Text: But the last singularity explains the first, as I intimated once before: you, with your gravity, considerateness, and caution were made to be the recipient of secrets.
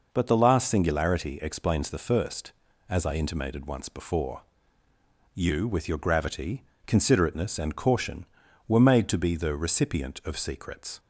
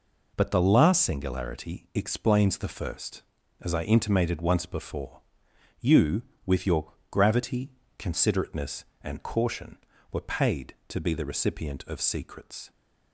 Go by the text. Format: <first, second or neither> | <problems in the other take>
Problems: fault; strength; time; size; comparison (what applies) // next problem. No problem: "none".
first | pauses between "your" and "gravity"; slight; at 6.9 s; 0.18 s long // says "paid" for "made"; at 10.2 s